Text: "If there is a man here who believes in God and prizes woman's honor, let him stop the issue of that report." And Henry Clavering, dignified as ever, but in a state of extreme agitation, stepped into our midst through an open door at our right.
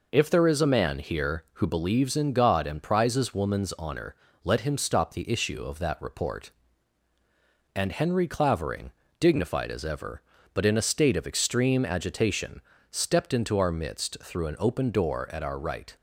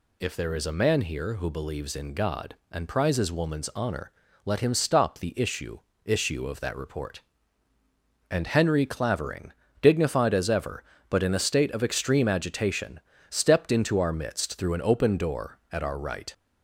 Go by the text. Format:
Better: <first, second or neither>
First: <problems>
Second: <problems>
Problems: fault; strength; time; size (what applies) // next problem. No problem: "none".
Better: first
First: none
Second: says "issue" twice; at 6.0 s